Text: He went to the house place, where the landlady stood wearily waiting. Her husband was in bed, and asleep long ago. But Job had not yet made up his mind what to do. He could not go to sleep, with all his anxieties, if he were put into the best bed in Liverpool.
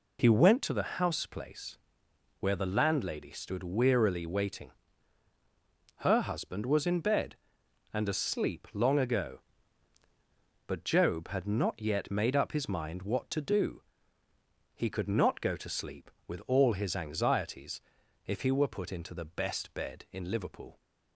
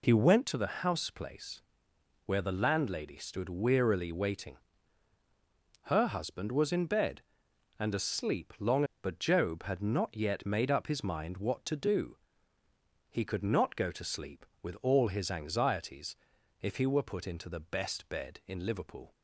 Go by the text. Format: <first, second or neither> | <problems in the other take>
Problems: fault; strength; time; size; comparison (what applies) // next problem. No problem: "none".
first | skips "ago"; at 8.9 s